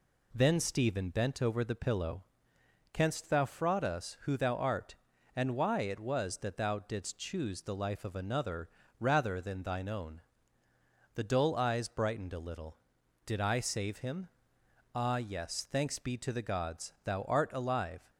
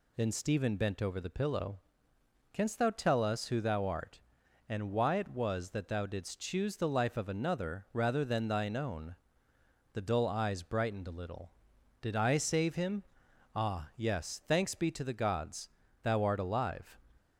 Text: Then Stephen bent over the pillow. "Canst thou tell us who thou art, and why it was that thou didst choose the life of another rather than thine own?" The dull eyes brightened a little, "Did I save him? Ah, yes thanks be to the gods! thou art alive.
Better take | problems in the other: second | says "fraud" for "tell"; at 3.4 s // pauses between "another" and "rather"; slight; at 8.6 s; 0.28 s long

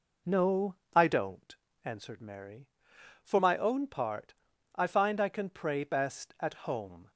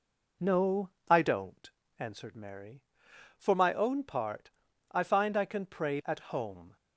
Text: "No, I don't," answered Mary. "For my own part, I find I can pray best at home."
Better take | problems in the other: first | skips "best"; at 6.0 s

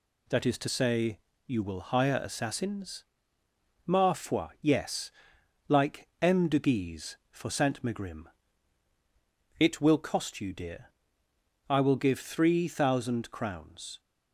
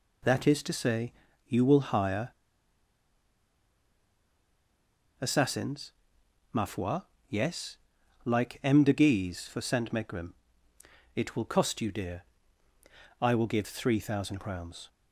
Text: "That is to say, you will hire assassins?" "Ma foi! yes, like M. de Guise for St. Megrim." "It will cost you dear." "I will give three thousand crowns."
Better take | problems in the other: first | pauses between "hire" and "assassins"; strong; at 2.3 s; 2.8 s long

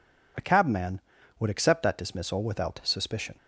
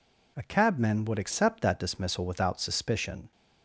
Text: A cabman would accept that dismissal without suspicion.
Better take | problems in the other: neither | none

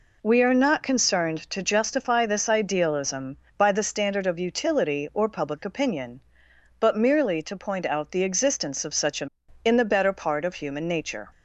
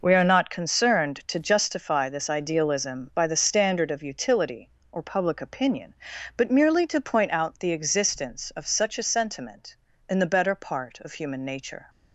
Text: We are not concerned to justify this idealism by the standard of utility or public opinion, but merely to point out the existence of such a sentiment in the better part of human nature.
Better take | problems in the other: second | skips "sentiment"; at 9.4 s

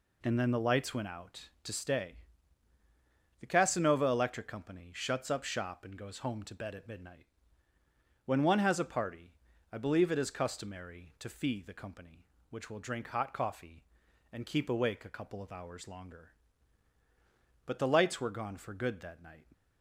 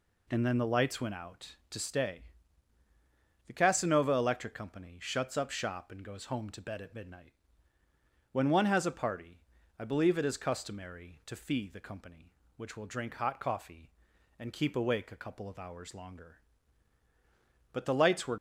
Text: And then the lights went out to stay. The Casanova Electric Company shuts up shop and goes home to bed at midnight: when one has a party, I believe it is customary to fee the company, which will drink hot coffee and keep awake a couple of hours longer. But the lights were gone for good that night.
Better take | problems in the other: first | stops before "gone for good that night"; at 18.3 s

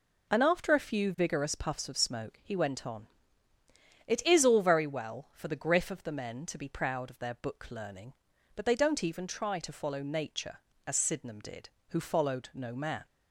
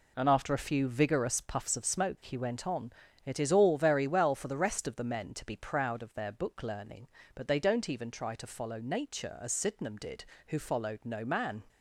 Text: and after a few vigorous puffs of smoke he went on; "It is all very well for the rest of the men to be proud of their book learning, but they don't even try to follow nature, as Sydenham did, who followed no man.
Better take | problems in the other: second | says "griff" for "rest"; at 5.5 s

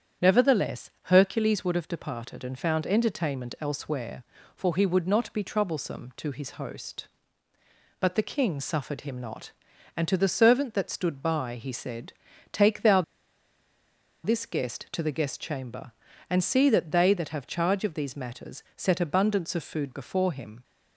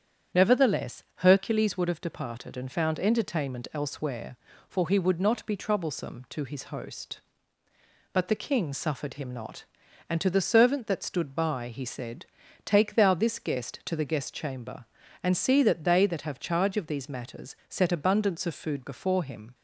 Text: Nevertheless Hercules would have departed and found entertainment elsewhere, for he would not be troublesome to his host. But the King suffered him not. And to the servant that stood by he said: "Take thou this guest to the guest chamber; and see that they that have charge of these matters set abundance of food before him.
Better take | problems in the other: second | starts louder than the rest; strong; until 1.3 s; 8.5 dB; strong in the second // pauses between "thou" and "this"; at 13.0 s; 1.2 s long

